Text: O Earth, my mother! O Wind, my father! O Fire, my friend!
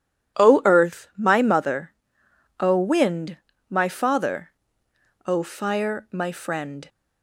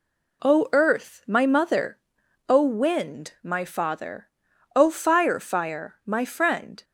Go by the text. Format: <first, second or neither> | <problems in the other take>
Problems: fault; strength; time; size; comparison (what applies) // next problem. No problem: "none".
first | says "Fire" twice; at 5.3 s